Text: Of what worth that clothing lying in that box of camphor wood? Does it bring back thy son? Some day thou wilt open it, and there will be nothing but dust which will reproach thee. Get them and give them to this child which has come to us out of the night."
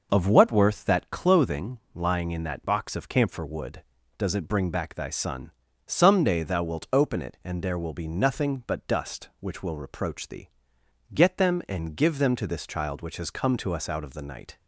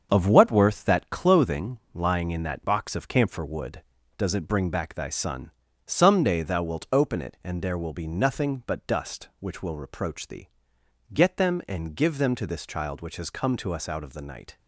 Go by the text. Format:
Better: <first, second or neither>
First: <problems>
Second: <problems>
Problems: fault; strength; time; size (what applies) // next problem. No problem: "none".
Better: first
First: pauses between "clothing" and "lying"; slight; at 1.7 s; 0.16 s long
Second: gets quieter; noticeable; throughout; 6 dB // pauses between "clothing" and "lying"; slight; at 1.7 s; 0.16 s long